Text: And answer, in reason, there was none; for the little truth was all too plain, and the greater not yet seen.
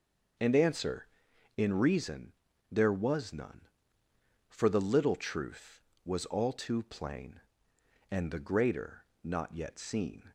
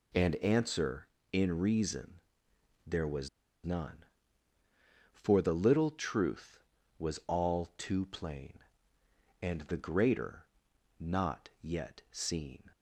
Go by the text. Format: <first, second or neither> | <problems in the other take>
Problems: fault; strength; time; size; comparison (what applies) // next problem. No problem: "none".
first | pauses between "was" and "none"; at 3.2 s; 0.36 s long // pauses between "greater" and "not"; noticeable; at 10.4 s; 0.52 s long; slight in the first